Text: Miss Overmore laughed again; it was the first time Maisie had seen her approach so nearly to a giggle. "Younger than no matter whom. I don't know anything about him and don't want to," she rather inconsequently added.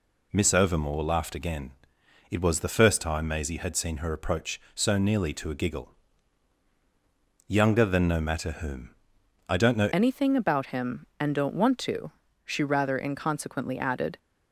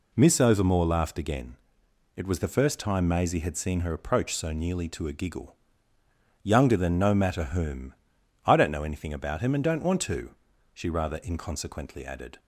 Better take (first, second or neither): second